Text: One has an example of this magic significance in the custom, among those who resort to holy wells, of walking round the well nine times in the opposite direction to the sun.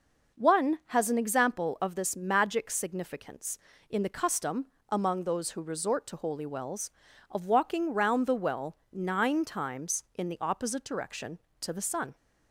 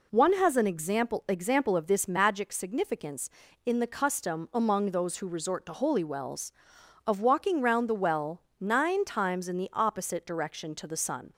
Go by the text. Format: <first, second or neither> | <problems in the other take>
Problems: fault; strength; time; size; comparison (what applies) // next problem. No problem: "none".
first | says "example" twice; at 1.2 s // pauses between "well" and "nine"; slight; at 8.4 s; 0.18 s long; slight in the first